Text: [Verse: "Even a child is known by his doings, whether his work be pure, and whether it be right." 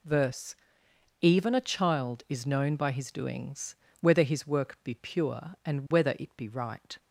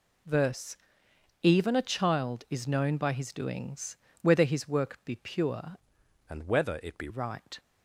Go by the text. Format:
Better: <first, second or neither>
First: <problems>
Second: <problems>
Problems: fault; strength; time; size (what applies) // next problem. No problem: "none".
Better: first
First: none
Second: changes voice from "and" to "be"; from 6.2 to 7.0 s; 0.8 s long